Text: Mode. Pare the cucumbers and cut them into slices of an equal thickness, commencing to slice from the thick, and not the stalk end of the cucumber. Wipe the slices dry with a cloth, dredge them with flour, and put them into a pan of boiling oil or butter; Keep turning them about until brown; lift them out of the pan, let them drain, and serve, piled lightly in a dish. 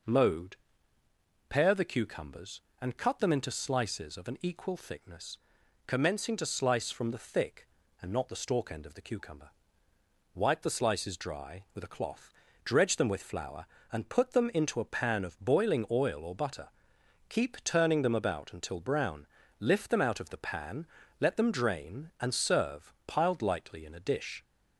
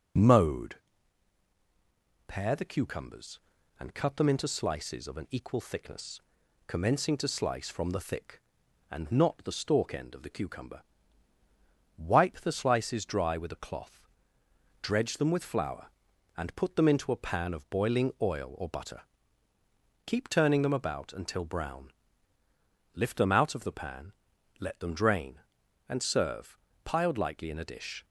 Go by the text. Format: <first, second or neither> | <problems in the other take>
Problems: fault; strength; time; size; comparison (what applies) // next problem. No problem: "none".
neither | none